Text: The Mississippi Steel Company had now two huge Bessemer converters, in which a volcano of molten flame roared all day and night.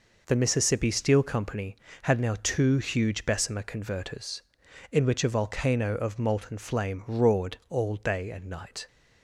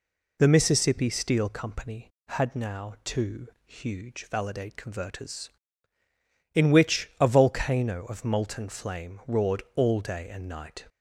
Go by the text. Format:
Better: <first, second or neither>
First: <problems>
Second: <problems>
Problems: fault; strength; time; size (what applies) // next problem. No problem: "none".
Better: first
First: none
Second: pauses between "two" and "huge"; slight; at 3.4 s; 0.18 s long // says "Validate" for "Bessemer"; at 4.2 s